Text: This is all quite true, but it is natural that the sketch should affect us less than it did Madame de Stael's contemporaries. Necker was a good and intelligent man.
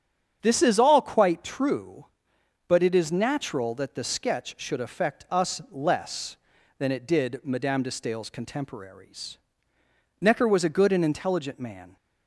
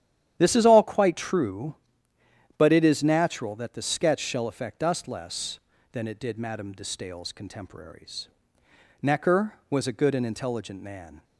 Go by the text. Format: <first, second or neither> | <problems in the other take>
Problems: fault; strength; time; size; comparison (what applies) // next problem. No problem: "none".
first | starts louder than the rest; strong; until 1.4 s; 10.5 dB; strong in the first // says "shall" for "should"; at 4.1 s